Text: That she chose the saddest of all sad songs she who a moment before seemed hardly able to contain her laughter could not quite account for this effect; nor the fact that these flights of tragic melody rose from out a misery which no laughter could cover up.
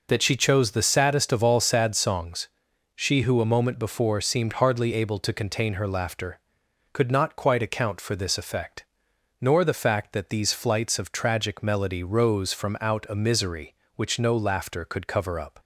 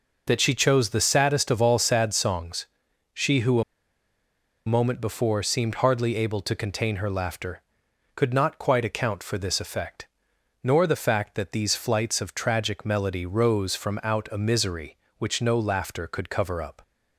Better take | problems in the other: first | pauses between "songs" and "she"; noticeable; at 2.6 s; 0.48 s long; noticeable in the first // pauses between "who" and "a"; at 3.6 s; 1.0 s long

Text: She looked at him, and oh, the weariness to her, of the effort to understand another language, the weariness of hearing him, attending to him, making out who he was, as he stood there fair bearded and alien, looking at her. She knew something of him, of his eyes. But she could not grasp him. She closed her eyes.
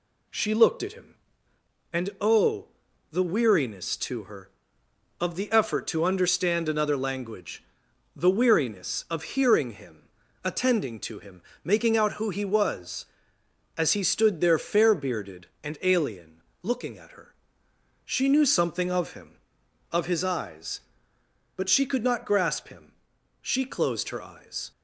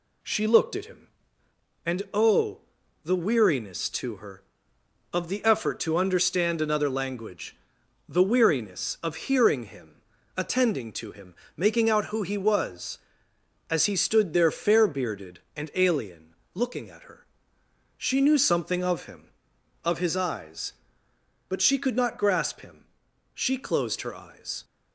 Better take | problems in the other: neither | none

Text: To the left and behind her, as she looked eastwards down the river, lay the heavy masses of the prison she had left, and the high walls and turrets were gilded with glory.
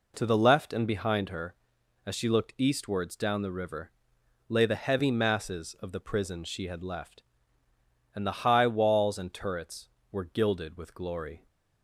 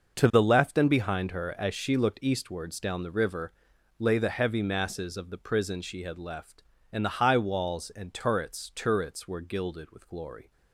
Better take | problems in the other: first | starts louder than the rest; noticeable; until 1.2 s; 6 dB // says "turrets" twice; at 8.7 s

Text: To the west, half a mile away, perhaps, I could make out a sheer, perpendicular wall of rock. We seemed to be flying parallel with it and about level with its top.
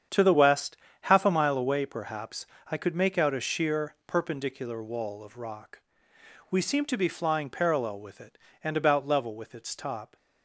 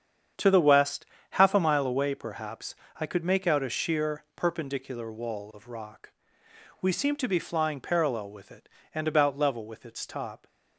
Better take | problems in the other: neither | starts louder than the rest; strong; the same in both

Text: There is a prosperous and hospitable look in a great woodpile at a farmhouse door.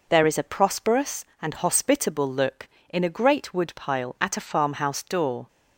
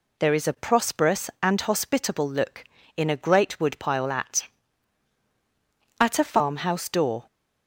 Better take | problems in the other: first | says "at" twice; at 6.0 s

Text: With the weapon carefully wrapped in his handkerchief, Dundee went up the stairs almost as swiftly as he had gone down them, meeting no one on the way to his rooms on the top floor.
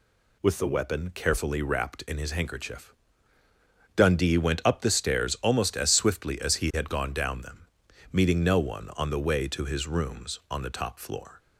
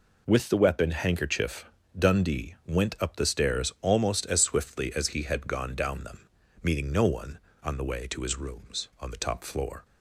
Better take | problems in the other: first | skips "carefully wrapped in his"; at 0.9 s

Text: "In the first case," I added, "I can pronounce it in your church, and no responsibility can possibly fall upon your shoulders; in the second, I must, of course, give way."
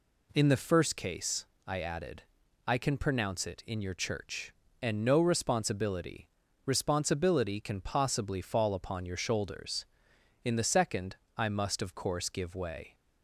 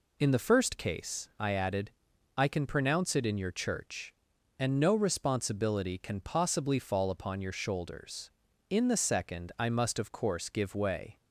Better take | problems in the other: second | says "responsibility" twice; at 6.6 s

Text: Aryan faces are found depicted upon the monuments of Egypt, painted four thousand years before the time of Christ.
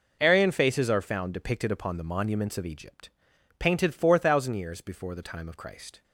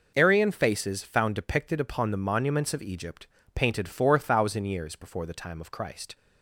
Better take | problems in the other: first | skips "are"; at 1.0 s

